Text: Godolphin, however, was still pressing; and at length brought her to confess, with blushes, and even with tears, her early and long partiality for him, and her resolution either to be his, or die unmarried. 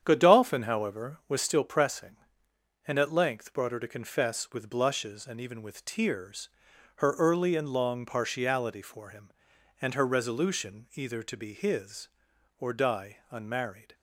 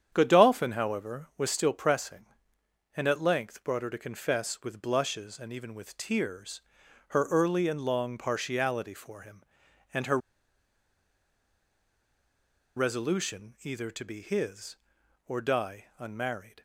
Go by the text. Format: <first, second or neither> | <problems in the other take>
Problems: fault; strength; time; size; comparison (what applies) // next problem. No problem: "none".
first | starts louder than the rest; strong; until 1.1 s; 8.5 dB; strong in the first // pauses between "her" and "resolution"; strong; at 10.1 s; 2.5 s long